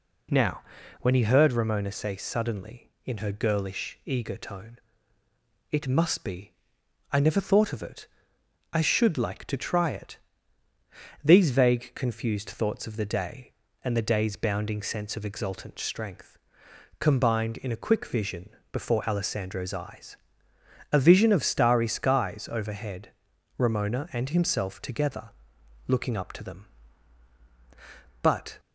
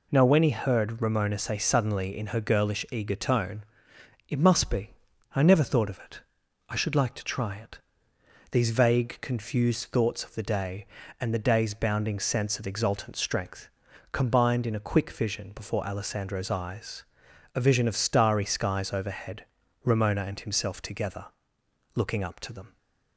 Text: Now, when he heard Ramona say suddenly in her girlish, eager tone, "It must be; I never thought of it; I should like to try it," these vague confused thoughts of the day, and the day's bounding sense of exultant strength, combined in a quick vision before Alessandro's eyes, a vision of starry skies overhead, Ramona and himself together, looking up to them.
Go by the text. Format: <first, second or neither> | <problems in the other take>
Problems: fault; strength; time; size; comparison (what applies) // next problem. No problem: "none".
second | pauses between "vision" and "before"; slight; at 18.4 s; 0.22 s long // goes on to say "But"; slight; from 28.2 s on; 0.38 s long